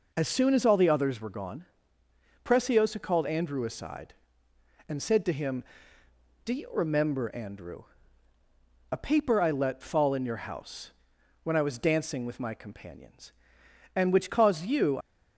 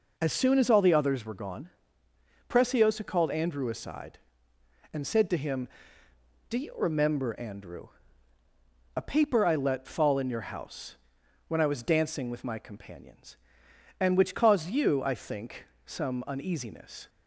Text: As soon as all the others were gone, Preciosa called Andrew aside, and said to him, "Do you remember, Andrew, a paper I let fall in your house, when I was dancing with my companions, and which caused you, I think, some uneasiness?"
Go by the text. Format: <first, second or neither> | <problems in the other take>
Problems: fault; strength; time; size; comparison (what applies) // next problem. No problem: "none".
second | stops before "I think some uneasiness"; at 15.0 s